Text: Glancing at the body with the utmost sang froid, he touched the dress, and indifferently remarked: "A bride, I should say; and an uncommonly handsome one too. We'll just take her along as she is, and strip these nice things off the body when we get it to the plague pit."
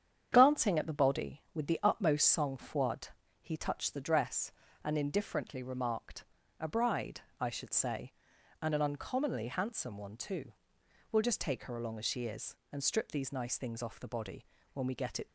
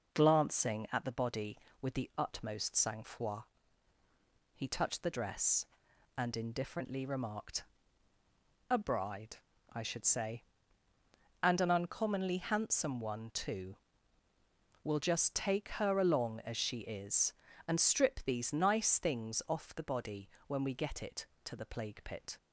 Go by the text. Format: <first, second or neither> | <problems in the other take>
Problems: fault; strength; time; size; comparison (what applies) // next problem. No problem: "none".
second | starts louder than the rest; strong; until 1.3 s; 8.5 dB // pauses between "body" and "when"; slight; at 14.4 s; 0.26 s long; slight in the second // stops before "to the plague pit"; at 15.2 s